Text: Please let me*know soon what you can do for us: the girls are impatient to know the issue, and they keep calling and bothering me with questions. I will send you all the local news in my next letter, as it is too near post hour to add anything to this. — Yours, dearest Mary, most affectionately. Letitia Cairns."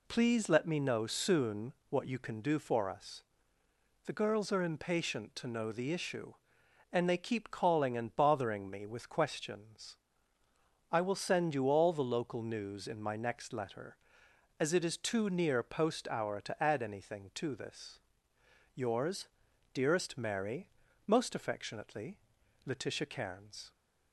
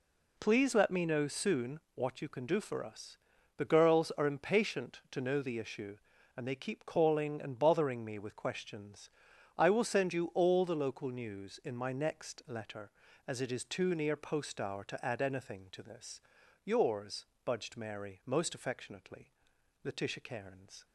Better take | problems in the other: first | pauses between "soon" and "what"; slight; at 1.7 s; 0.16 s long; slight in the first // says "budged" for "dearest"; at 17.4 s

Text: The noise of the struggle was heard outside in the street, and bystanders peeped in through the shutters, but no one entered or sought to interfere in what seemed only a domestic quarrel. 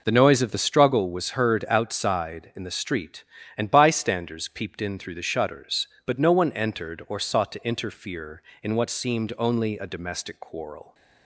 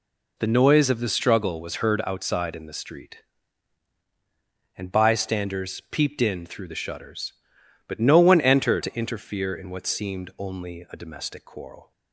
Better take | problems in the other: first | skips "or sought"; at 8.8 s

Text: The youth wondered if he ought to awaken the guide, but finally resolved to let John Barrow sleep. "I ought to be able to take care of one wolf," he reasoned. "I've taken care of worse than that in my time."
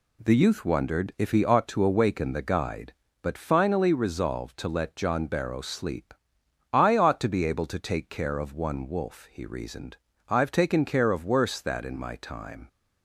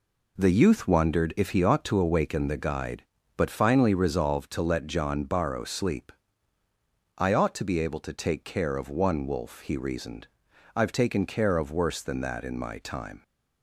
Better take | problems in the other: second | skips "than"; at 11.6 s

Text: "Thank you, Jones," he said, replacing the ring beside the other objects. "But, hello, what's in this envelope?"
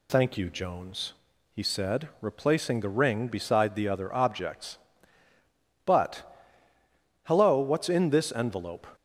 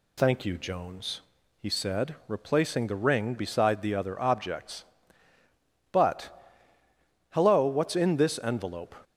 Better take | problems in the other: neither | none

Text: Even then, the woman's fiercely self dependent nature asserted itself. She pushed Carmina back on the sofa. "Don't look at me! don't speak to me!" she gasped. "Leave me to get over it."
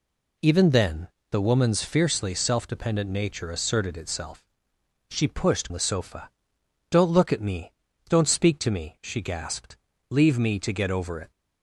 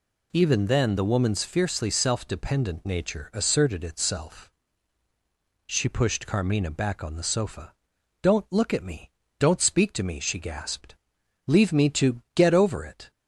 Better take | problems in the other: second | skips "Carmina back on"; at 5.6 s

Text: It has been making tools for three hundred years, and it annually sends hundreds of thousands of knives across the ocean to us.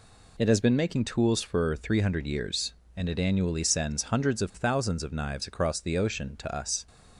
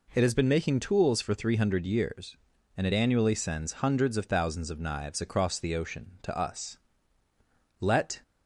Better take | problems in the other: first | goes on to say "Let"; slight; from 7.8 s on; 0.40 s long

